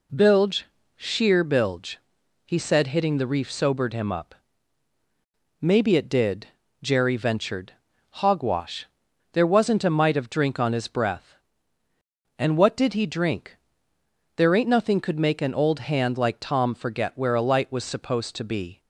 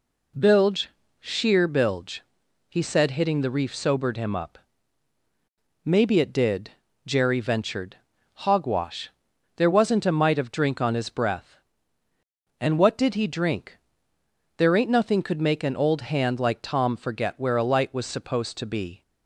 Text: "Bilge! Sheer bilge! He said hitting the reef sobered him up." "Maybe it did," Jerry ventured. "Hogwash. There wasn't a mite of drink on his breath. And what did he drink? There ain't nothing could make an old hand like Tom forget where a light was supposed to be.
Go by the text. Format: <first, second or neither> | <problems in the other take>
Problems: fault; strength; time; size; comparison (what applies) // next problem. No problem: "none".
neither | none